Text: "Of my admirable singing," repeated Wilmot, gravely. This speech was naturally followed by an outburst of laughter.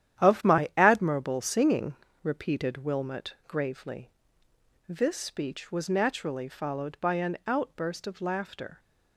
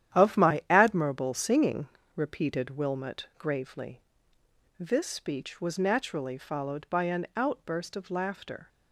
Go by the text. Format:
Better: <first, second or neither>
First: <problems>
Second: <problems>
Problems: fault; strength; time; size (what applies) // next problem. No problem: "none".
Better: neither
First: starts louder than the rest; strong; until 1.3 s; 11 dB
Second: starts louder than the rest; strong; until 1.2 s; 11 dB